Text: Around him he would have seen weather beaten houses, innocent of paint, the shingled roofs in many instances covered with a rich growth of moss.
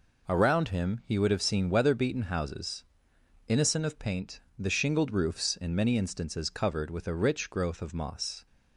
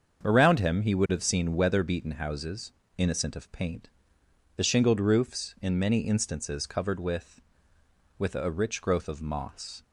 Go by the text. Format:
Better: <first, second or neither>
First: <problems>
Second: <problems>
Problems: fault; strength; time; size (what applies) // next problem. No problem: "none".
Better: first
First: none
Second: starts louder than the rest; until 1.2 s; 7 dB // says "with" twice; at 8.1 s